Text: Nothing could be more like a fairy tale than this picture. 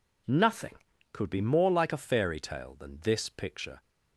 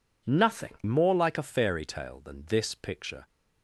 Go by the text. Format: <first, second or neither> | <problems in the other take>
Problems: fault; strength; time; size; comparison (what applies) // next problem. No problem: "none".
first | skips "could be"; at 0.8 s